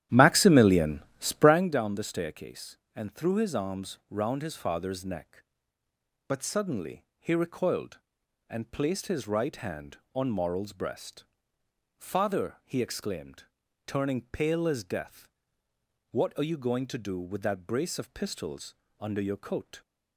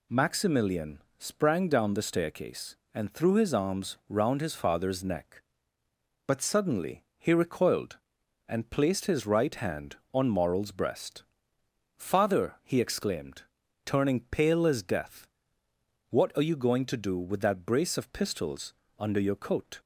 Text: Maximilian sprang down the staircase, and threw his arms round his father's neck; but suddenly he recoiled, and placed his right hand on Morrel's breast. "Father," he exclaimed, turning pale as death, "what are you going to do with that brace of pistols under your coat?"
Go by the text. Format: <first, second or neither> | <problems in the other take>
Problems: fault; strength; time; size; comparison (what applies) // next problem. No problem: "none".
second | starts louder than the rest; strong; until 1.7 s; 12 dB // pauses between "Maximilian" and "sprang"; slight; at 1.0 s; 0.16 s long; slight in the second // pauses between "pistols" and "under"; slight; at 18.7 s; 0.24 s long; slight in the second